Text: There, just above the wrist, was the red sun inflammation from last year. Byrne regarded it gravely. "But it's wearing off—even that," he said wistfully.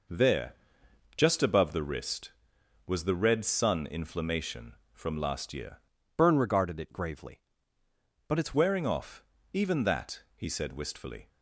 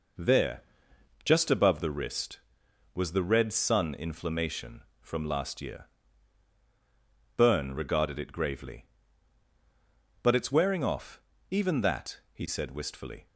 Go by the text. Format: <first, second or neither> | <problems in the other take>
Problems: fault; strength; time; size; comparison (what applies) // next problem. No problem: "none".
second | changes voice from "Byrne" to "it's"; from 6.1 to 8.5 s; 2.4 s long